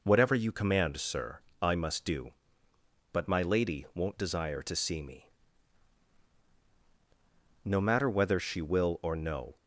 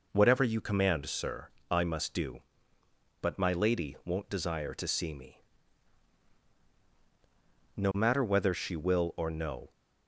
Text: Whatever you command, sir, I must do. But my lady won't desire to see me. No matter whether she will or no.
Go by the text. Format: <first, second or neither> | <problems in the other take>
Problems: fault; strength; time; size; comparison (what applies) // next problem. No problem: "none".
neither | none